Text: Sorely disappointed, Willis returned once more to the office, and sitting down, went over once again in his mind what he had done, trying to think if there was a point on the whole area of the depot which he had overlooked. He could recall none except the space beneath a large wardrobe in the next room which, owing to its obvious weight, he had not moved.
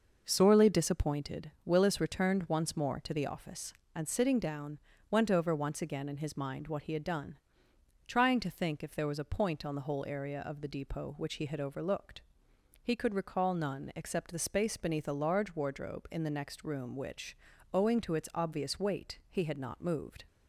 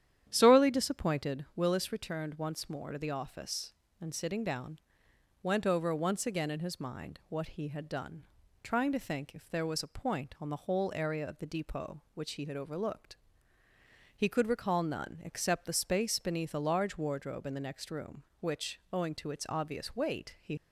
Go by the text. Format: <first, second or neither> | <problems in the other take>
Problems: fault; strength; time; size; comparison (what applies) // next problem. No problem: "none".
first | starts louder than the rest; strong; until 1.2 s; 10 dB // stops before "had not moved"; at 20.5 s